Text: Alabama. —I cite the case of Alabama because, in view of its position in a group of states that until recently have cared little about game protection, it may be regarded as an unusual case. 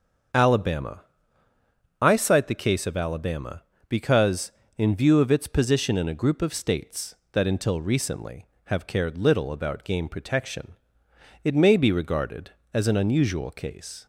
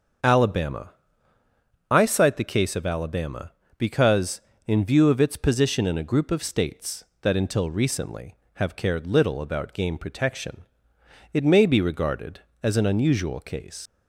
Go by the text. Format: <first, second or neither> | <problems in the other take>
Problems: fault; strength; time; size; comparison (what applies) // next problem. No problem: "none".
first | starts louder than the rest; until 2.2 s; 7 dB; also in the first // leaves "case" unfinished; at 13.8 s; 95 ms